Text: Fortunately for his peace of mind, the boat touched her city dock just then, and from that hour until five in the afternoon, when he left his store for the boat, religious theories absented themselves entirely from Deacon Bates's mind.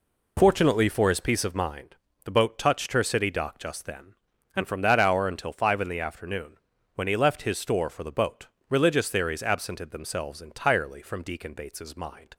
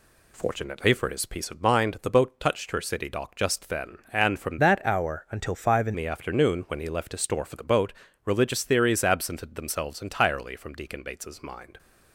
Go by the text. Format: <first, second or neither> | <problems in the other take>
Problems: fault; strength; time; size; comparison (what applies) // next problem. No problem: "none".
first | changes voice from "that" to "in"; from 4.5 to 5.9 s; 1.4 s long